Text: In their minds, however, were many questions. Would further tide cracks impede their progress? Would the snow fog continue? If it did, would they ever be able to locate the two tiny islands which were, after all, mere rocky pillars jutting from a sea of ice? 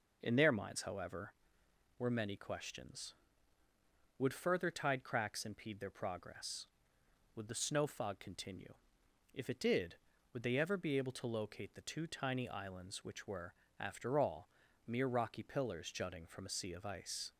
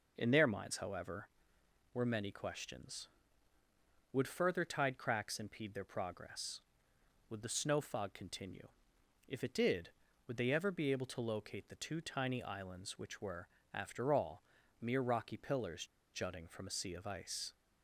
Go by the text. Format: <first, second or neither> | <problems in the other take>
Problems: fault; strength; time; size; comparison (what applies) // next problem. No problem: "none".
first | pauses between "pillars" and "jutting"; slight; at 15.8 s; 0.30 s long